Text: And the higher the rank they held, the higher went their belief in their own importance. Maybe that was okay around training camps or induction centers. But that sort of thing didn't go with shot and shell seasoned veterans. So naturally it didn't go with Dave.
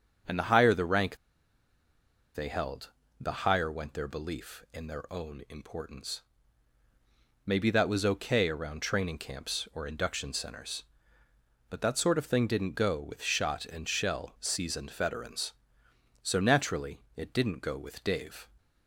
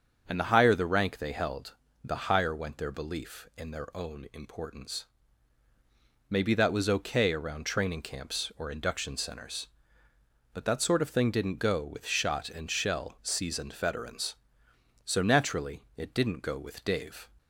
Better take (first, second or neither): second